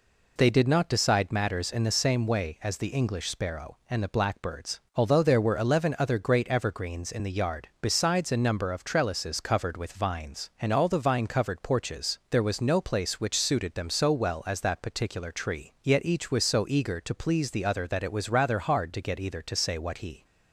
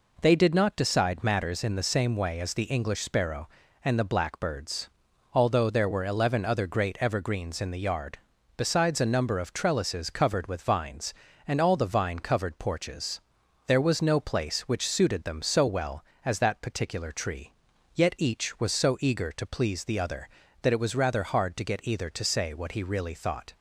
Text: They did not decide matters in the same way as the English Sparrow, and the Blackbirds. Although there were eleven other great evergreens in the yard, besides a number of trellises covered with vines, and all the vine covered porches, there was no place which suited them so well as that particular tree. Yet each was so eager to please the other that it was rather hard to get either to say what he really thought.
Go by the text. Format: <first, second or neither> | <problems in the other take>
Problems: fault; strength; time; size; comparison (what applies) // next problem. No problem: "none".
second | stops before "really thought"; at 20.2 s